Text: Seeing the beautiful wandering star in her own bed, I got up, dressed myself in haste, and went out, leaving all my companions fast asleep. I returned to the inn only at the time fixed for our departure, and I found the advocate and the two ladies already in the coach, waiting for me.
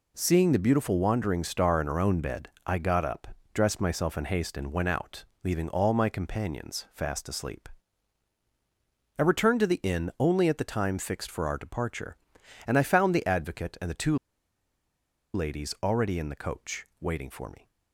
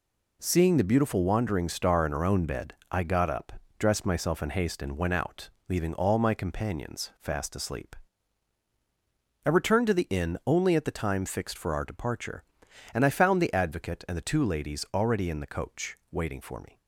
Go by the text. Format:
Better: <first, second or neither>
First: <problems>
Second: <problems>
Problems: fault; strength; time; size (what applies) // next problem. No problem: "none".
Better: second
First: pauses between "two" and "ladies"; at 14.1 s; 1.1 s long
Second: none